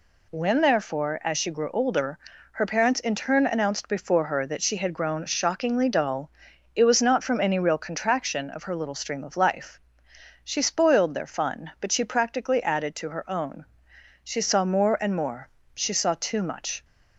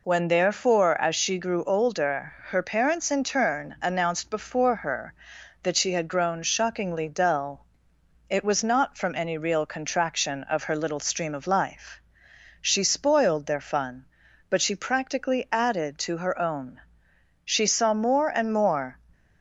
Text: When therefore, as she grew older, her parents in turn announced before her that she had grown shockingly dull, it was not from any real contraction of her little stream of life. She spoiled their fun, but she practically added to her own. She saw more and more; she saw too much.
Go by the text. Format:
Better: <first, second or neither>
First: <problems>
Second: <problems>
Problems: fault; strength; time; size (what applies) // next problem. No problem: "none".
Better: first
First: none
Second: stops before "she saw too much"; at 19.1 s